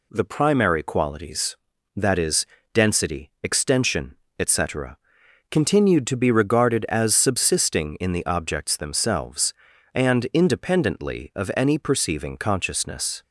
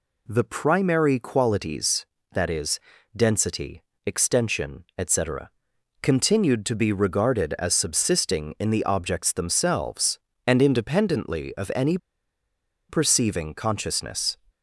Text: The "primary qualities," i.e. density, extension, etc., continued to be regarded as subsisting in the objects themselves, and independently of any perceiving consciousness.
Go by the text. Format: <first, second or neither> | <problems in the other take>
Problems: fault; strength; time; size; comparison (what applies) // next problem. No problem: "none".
first | pauses between "any" and "perceiving"; noticeable; at 11.9 s; 0.92 s long